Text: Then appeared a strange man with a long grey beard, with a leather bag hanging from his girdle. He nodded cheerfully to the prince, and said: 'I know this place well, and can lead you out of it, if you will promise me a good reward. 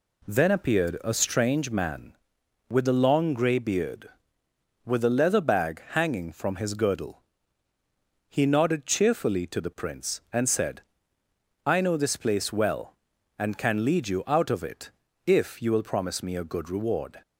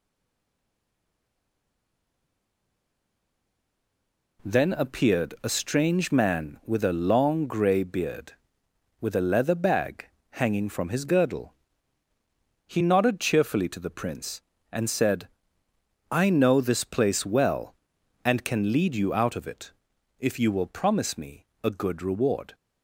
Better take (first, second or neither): first